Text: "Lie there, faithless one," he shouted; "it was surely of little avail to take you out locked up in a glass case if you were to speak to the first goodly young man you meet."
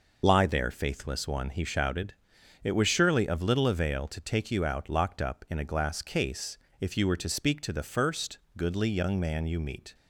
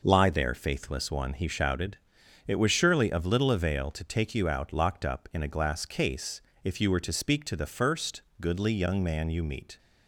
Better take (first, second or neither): second